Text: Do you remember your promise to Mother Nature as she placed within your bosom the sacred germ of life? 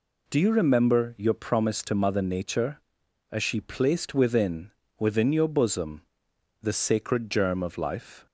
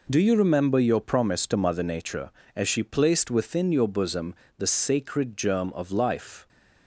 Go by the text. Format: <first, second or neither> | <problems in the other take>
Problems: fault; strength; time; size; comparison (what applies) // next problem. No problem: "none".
second | says "within" twice; at 4.9 s // pauses between "bosom" and "the"; noticeable; at 6.0 s; 0.58 s long; slight in the second